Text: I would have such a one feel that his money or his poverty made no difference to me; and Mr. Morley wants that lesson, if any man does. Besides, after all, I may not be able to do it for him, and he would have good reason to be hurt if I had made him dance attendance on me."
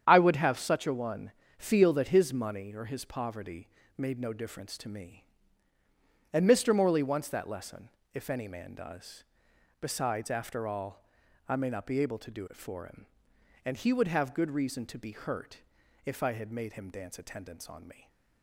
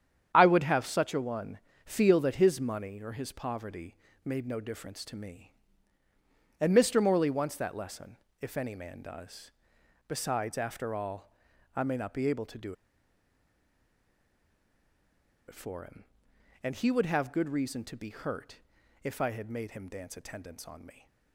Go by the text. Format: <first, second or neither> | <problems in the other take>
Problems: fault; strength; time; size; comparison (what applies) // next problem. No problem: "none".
first | starts louder than the rest; strong; until 1.3 s; 9 dB; strong in the first // pauses between "one" and "feel"; slight; at 1.5 s; 0.28 s long; slight in the first // pauses between "poverty" and "made"; slight; at 3.9 s; 0.30 s long; slight in the first // pauses between "do" and "it"; strong; at 12.7 s; 2.7 s long // pauses between "hurt" and "if"; noticeable; at 18.5 s; 0.46 s long; noticeable in the first